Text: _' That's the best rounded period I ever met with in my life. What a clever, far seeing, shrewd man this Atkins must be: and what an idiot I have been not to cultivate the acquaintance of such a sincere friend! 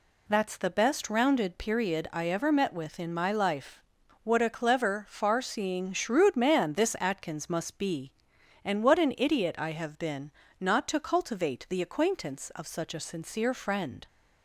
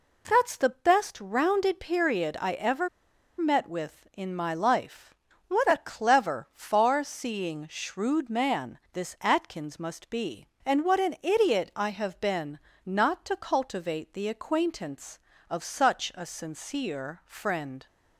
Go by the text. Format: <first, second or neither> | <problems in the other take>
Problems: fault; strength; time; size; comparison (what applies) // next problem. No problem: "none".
first | pauses between "ever" and "met"; noticeable; at 2.8 s; 0.51 s long // pauses between "been" and "not"; slight; at 12.5 s; 0.24 s long; slight in the first